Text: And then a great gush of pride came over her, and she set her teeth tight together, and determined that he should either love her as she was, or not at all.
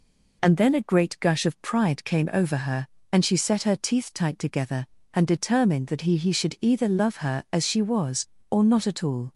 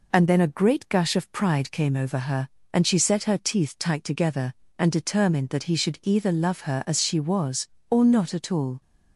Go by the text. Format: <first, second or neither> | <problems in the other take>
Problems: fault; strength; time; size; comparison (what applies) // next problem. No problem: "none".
second | says "he" twice; at 6.1 s